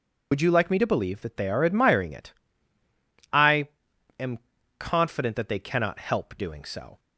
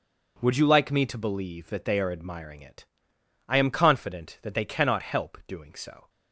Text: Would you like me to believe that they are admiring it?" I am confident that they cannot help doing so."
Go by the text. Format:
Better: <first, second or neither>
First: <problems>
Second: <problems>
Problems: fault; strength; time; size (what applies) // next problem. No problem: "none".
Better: second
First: loses the start of "Would"; at 0.3 s; 65 ms // pauses between "I" and "am"; noticeable; at 3.6 s; 0.50 s long // pauses between "am" and "confident"; at 4.3 s; 0.38 s long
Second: none